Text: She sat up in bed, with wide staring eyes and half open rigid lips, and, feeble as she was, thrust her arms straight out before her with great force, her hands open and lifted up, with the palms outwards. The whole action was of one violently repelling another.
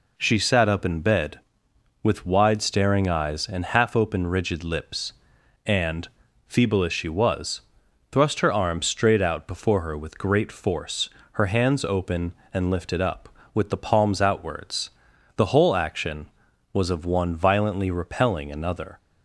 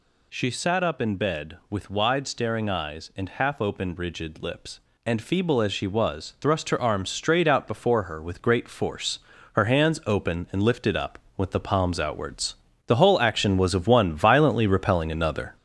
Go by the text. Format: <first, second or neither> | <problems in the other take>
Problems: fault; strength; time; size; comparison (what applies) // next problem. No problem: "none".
first | gets louder; noticeable; throughout; 5 dB